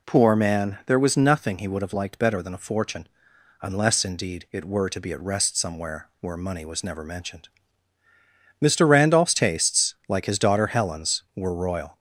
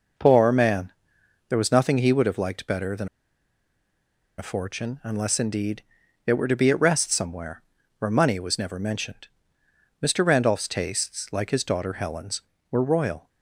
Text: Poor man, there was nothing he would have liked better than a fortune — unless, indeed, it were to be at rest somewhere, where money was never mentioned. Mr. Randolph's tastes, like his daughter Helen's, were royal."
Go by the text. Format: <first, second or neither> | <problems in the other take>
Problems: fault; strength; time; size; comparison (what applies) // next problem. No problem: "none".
first | pauses between "than" and "a"; strong; at 3.0 s; 1.3 s long